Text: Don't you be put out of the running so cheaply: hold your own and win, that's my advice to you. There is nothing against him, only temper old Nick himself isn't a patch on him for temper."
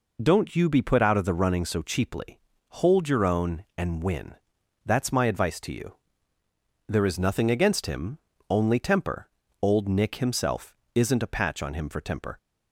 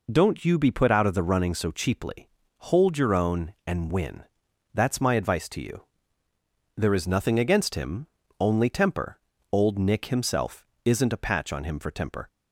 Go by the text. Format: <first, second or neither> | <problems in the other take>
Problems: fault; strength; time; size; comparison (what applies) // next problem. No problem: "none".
neither | pauses between "temper" and "old"; slight; the same in both // pauses between "himself" and "isn't"; slight; the same in both